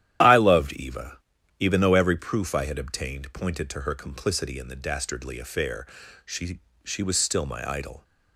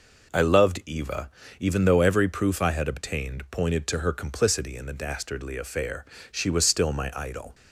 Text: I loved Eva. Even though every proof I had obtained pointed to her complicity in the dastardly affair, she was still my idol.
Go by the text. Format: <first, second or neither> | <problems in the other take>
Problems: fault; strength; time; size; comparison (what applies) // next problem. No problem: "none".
second | starts louder than the rest; strong; until 1.6 s; 11.5 dB // says "she" twice; at 6.8 s